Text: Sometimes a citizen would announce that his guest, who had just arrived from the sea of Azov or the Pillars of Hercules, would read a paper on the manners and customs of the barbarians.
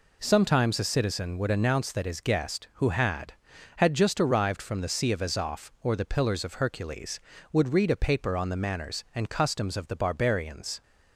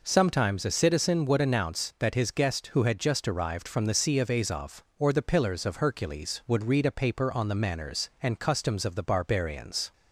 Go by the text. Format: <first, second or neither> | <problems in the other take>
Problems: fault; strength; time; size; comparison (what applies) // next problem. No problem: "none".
second | says "had" twice; at 3.7 s